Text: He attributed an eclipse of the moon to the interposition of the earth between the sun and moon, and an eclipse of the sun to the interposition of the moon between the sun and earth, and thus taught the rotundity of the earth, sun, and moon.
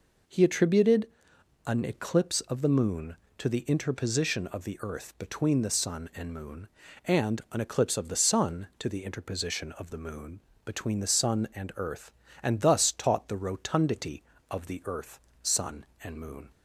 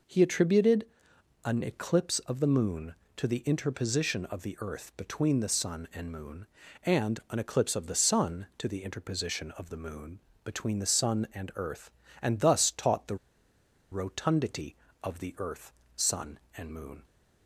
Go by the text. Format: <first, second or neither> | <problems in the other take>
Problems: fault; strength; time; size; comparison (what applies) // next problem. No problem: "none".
first | pauses between "attributed" and "an"; noticeable; at 0.8 s; 0.60 s long; noticeable in the first // pauses between "moon" and "between"; slight; at 10.1 s; 0.24 s long; slight in the first // pauses between "the" and "rotundity"; noticeable; at 13.1 s; 0.75 s long